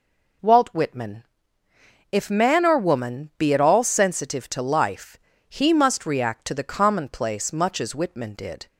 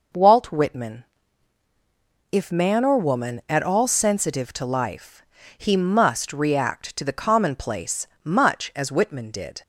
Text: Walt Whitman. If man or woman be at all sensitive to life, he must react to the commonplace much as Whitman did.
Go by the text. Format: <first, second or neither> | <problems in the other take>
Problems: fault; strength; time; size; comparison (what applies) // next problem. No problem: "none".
first | skips "be"; at 3.4 s // pauses between "commonplace" and "much"; slight; at 8.0 s; 0.18 s long